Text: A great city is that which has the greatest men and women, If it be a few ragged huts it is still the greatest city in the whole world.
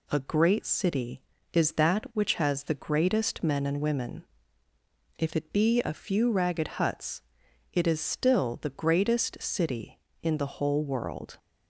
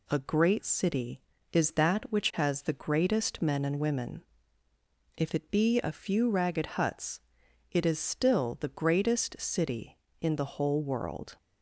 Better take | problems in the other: neither | pauses between "huts" and "it"; noticeable; the same in both

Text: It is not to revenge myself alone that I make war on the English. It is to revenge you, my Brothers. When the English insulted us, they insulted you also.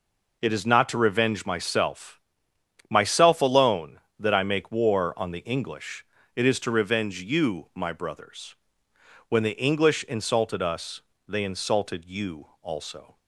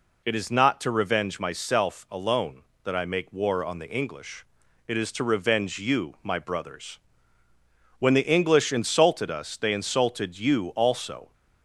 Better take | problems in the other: second | says "myself" twice; at 2.8 s // pauses between "you" and "also"; slight; at 12.4 s; 0.16 s long

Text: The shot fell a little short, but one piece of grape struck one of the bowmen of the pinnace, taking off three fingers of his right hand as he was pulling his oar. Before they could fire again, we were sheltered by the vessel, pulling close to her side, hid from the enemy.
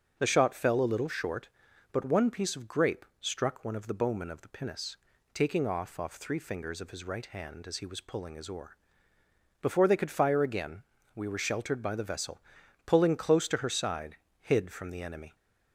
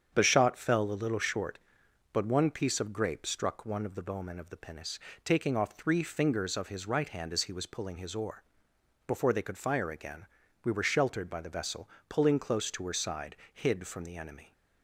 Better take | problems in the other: second | starts louder than the rest; until 1.2 s; 7 dB; strong in the second // says "off" twice; at 5.9 s

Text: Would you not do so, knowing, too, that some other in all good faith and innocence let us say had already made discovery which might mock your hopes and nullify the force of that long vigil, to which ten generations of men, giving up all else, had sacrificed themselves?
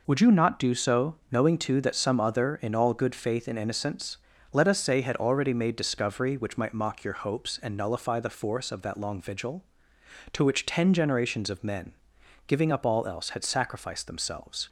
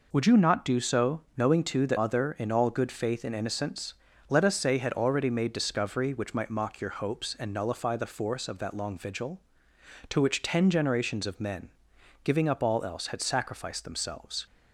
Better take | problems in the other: first | skips "some"; at 1.9 s // pauses between "innocence" and "let"; slight; at 3.9 s; 0.36 s long; slight in the first

